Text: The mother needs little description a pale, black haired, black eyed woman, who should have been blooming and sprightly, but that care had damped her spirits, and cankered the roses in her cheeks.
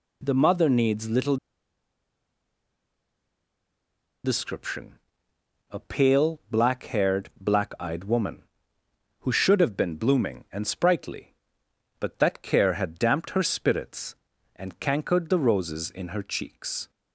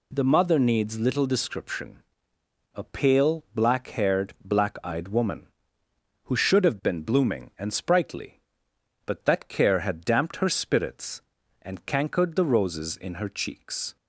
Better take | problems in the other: second | pauses between "little" and "description"; strong; at 1.3 s; 2.8 s long // pauses between "description" and "a"; noticeable; at 4.9 s; 0.74 s long; noticeable in the second

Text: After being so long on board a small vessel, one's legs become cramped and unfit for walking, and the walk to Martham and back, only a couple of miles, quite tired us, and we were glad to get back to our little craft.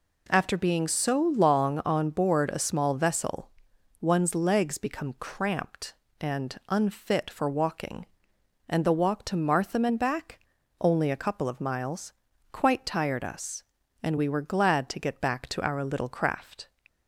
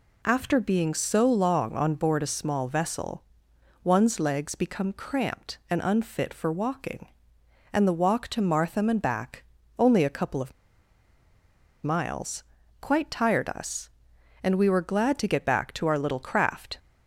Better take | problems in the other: first | pauses between "of" and "miles"; strong; at 10.5 s; 1.3 s long

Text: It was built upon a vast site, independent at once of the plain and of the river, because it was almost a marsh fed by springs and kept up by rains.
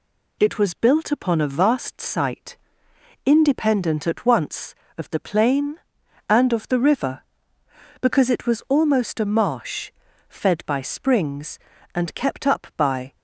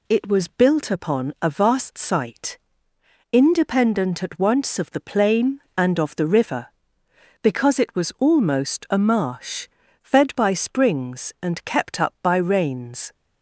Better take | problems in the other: second | pauses between "marsh" and "fed"; slight; at 9.9 s; 0.36 s long; slight in the second // stops before "rains"; at 13.1 s

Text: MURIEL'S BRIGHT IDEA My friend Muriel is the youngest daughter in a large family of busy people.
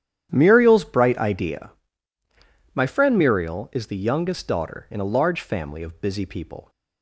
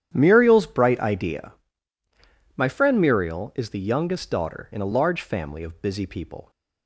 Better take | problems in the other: neither | starts louder than the rest; strong; the same in both // pauses between "IDEA" and "My"; the same in both

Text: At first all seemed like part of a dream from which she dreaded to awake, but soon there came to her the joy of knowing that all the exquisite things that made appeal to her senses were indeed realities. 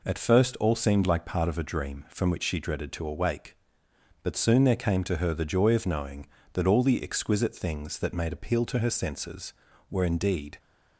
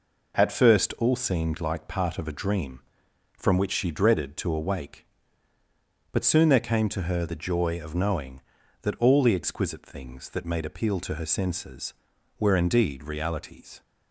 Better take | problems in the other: second | stops before "realities"; at 10.5 s

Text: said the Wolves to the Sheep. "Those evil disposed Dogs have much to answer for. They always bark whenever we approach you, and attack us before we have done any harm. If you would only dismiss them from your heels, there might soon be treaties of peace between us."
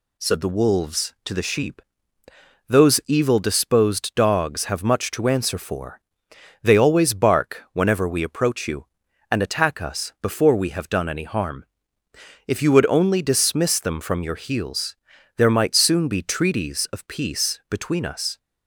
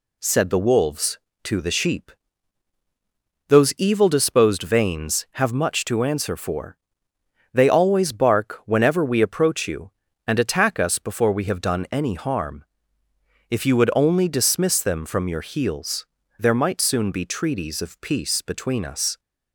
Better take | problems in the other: first | says "Vanes" for "Dogs"; at 4.6 s

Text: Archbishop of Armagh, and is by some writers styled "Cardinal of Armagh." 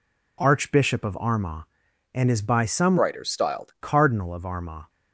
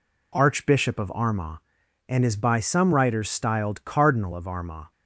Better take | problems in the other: second | changes voice from "writers" to "styled"; from 2.9 to 3.7 s; 0.8 s long

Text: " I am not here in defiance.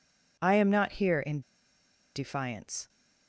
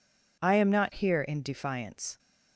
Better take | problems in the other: second | pauses between "in" and "defiance"; noticeable; at 1.4 s; 0.74 s long

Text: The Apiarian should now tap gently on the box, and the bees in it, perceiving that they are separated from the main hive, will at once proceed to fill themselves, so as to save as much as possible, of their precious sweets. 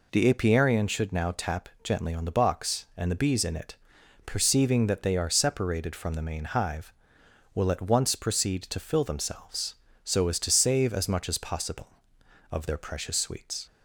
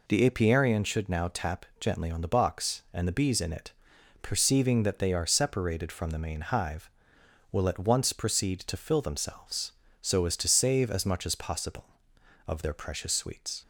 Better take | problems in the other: neither | pauses between "tap" and "gently"; slight; the same in both

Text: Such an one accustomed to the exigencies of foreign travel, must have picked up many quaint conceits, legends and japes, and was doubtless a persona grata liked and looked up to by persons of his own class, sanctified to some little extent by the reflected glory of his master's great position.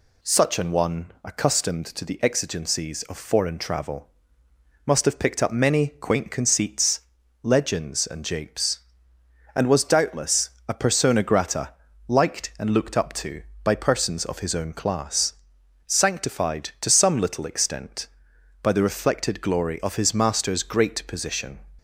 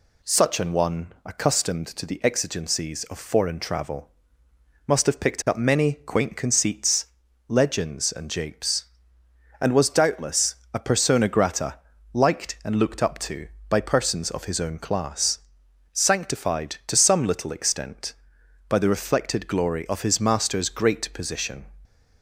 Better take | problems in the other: neither | pauses between "doubtless" and "a"; slight; the same in both // pauses between "grata" and "liked"; slight; the same in both

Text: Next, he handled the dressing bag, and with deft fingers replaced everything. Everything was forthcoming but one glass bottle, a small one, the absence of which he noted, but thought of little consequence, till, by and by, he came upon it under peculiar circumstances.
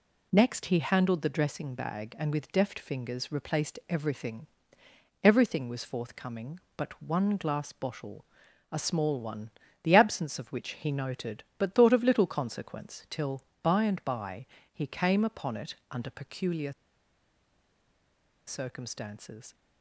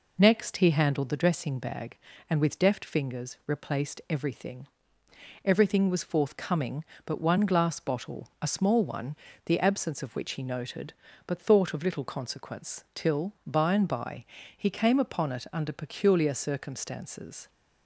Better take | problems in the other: second | pauses between "it" and "under"; slight; at 15.7 s; 0.16 s long // pauses between "peculiar" and "circumstances"; strong; at 16.7 s; 1.7 s long

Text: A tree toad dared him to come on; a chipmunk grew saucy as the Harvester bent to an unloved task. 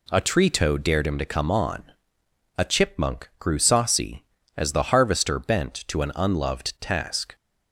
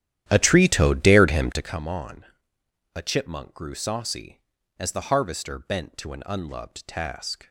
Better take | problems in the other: first | starts louder than the rest; strong; until 1.8 s; 11.5 dB

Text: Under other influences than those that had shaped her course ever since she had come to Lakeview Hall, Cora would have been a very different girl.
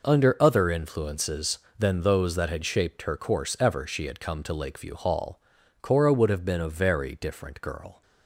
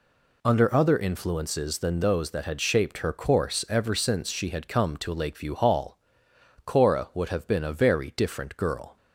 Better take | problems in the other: second | skips "since"; at 3.8 s

